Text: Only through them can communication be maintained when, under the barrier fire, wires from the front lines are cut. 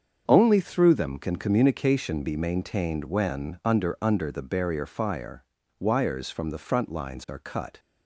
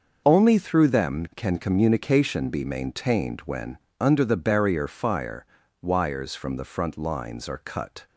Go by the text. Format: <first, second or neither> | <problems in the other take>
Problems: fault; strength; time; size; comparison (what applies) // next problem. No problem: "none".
second | starts louder than the rest; until 1.2 s; 7 dB; noticeable in the second // says "under" twice; at 4.0 s